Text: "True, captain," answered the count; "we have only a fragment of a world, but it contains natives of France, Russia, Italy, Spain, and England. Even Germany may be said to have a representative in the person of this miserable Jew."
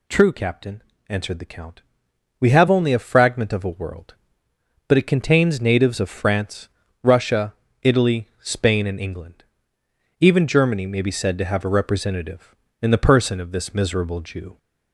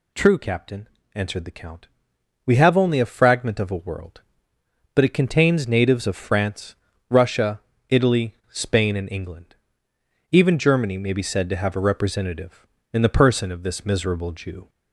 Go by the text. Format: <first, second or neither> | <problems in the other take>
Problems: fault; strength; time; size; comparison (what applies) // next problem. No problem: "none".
neither | none